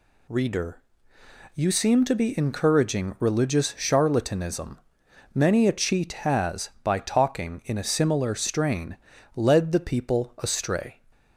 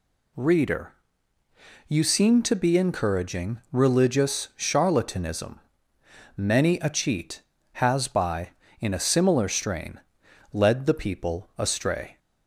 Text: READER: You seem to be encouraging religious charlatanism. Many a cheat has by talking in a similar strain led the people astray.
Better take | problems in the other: first | skips "talking"; at 8.6 s // pauses between "strain" and "led"; noticeable; at 9.9 s; 0.52 s long; slight in the first

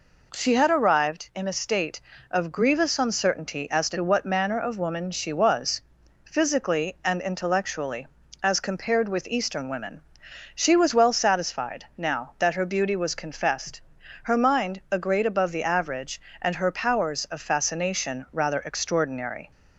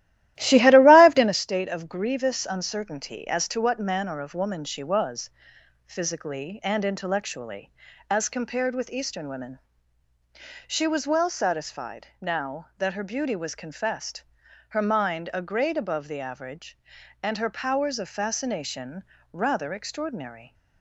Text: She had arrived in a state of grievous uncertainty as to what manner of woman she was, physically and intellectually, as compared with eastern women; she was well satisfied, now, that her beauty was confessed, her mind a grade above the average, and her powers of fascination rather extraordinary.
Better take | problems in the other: first | starts louder than the rest; strong; until 1.4 s; 14.5 dB // pauses between "fascination" and "rather"; slight; at 19.0 s; 0.28 s long

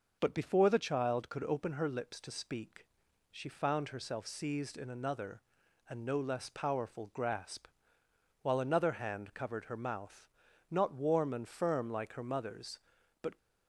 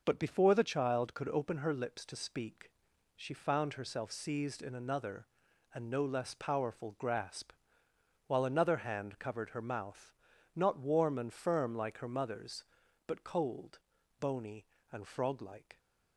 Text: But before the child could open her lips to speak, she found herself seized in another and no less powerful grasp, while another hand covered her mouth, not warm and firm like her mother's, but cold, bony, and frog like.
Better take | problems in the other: second | stops before "cold bony and frog like"; at 13.3 s

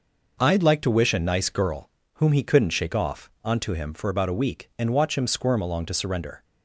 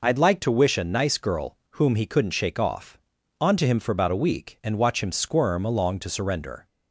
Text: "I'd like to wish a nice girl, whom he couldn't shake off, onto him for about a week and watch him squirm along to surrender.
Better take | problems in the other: neither | none

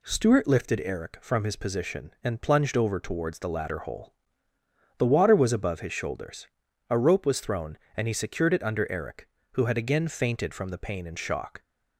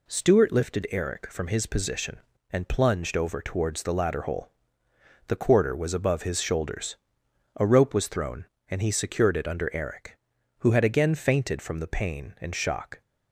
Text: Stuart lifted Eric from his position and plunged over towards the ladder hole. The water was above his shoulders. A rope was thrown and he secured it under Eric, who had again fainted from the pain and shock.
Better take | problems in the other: first | says "quarter" for "water"; at 5.3 s

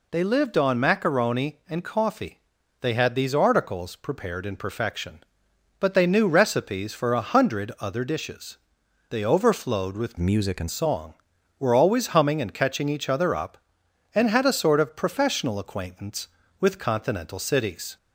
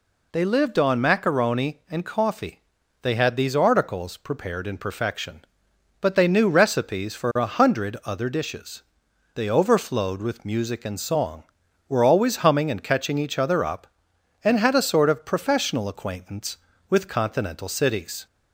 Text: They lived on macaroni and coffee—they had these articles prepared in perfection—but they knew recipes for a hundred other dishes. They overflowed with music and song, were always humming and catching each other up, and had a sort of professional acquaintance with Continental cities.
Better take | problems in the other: second | changes voice from "music" to "and"; from 10.1 to 10.6 s; 0.5 s long

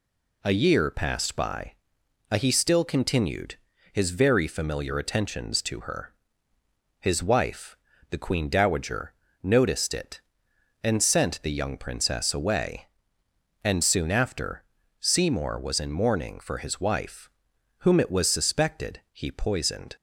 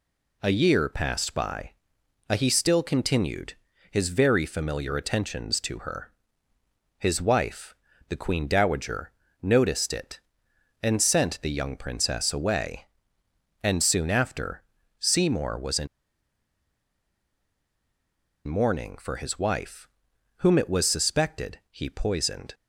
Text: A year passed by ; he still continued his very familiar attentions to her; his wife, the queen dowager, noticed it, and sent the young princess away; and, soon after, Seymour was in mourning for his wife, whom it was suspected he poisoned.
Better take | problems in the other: first | pauses between "continued" and "his"; slight; at 3.5 s; 0.36 s long; slight in the first // pauses between "in" and "mourning"; strong; at 15.8 s; 2.6 s long

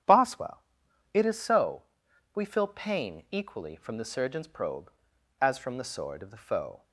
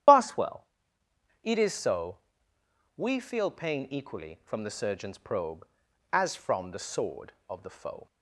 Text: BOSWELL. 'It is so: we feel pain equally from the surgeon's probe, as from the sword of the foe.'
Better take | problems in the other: first | loses the start of "BOSWELL"; at 0.0 s; 45 ms // starts louder than the rest; strong; until 1.8 s; 10.5 dB; strong in the first

